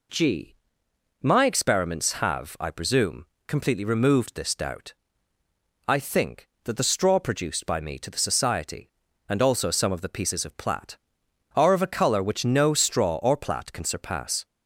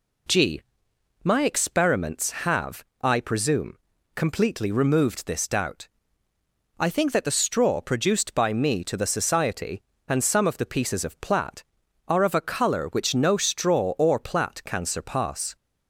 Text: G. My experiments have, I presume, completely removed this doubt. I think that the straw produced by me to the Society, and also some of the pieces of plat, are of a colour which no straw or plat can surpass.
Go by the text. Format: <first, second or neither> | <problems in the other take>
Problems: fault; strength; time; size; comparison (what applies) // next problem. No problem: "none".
first | skips "also"; at 10.2 s